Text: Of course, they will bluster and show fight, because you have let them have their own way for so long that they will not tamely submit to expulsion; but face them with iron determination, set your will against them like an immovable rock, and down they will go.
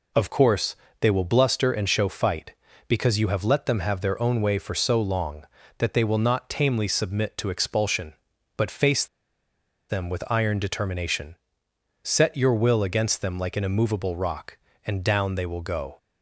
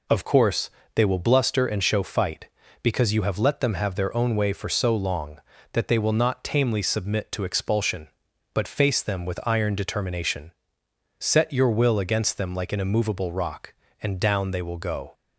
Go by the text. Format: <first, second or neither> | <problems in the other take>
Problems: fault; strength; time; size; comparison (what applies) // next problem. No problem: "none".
second | pauses between "face" and "them"; noticeable; at 9.0 s; 0.82 s long